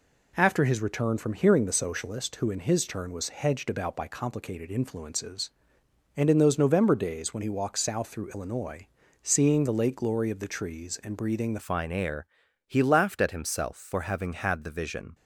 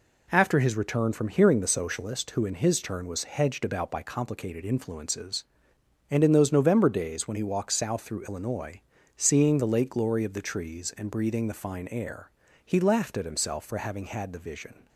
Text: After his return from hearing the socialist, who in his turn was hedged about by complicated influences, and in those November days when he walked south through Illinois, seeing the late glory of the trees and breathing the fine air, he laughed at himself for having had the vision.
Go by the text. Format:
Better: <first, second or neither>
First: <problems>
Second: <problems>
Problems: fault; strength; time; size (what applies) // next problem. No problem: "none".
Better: second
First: changes voice at "fine"; from 11.6 s on; 3.5 s long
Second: none